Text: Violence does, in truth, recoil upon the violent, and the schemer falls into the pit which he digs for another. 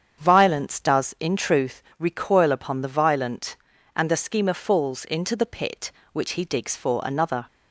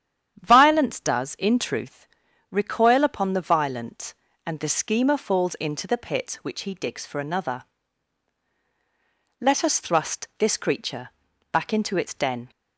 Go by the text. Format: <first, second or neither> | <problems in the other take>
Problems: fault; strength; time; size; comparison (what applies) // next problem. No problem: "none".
first | starts louder than the rest; strong; until 1.4 s; 9.5 dB; strong in the first // goes on to say "Let us thrust this creature back into its den"; strong; from 9.4 s on; 3.1 s long